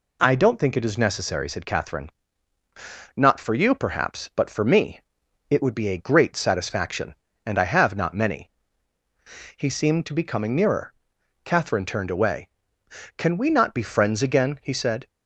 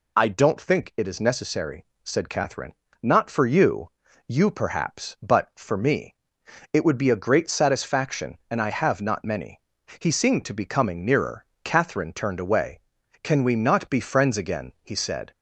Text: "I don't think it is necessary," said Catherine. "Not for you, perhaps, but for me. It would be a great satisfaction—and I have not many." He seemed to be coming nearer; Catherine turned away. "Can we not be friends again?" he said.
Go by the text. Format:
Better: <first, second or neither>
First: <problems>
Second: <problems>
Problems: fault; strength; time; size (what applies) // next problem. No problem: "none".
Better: first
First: none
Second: says "you" twice; at 4.2 s